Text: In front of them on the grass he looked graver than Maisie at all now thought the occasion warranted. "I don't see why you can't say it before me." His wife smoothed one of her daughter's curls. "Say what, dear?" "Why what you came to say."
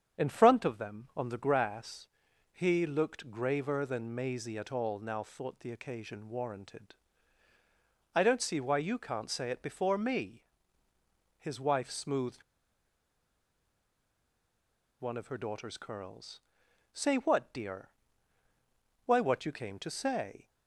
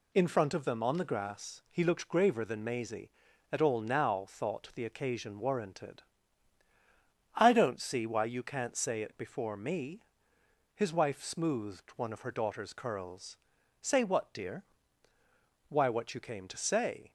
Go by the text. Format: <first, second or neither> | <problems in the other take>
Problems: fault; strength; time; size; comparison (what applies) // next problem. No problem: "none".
second | starts louder than the rest; strong; until 1.2 s; 7.5 dB // pauses between "grass" and "he"; noticeable; at 2.0 s; 0.48 s long // pauses between "smoothed" and "one"; strong; at 12.4 s; 2.5 s long